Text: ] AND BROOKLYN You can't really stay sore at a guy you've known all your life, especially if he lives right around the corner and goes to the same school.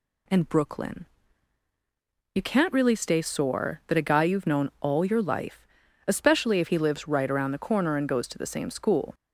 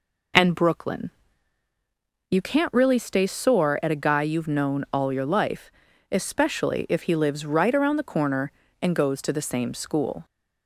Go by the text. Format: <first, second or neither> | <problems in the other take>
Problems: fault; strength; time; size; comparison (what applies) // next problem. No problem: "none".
second | pauses between "BROOKLYN" and "You"; strong; at 1.0 s; 1.2 s long; also in the second // says "that" for "at"; at 3.8 s